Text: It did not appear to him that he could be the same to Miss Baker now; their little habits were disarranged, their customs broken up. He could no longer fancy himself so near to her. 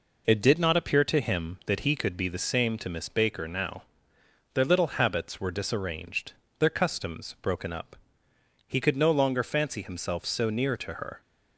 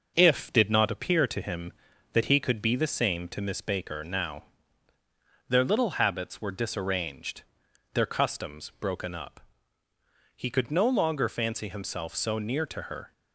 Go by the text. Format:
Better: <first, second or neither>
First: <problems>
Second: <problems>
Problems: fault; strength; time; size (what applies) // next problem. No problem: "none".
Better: first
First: none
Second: says "If" for "It"; at 0.1 s